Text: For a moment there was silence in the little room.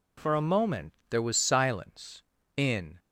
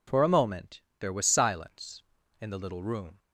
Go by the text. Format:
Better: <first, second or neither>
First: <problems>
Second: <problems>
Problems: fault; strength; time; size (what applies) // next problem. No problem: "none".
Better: second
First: pauses between "moment" and "there"; slight; at 0.9 s; 0.16 s long // stops before "the little room"; at 2.9 s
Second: pauses between "moment" and "there"; slight; at 0.8 s; 0.20 s long